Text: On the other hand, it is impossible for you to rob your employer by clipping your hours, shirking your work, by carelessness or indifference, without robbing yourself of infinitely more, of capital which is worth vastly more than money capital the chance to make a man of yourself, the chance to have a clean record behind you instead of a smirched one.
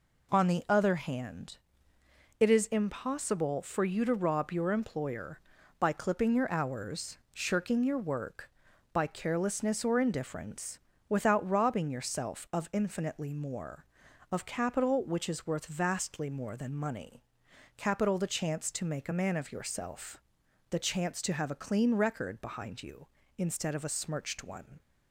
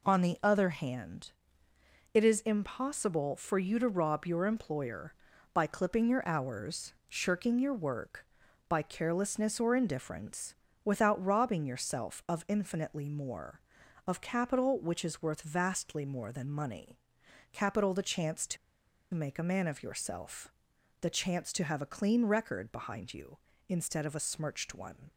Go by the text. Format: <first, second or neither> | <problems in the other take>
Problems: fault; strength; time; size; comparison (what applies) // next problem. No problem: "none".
first | pauses between "money" and "capital"; noticeable; at 16.9 s; 0.56 s long; noticeable in the first // pauses between "to" and "make"; noticeable; at 18.5 s; 0.57 s long